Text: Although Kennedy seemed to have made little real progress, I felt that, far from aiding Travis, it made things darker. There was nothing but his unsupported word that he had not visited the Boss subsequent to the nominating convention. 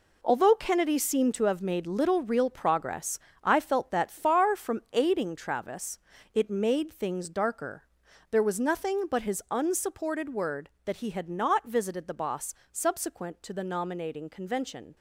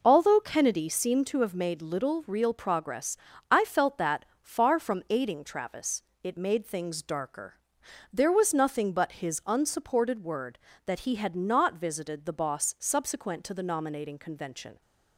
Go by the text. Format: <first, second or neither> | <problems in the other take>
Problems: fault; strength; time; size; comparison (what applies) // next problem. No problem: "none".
second | gets quieter; strong; throughout; 10 dB // pauses between "Boss" and "subsequent"; slight; at 12.5 s; 0.18 s long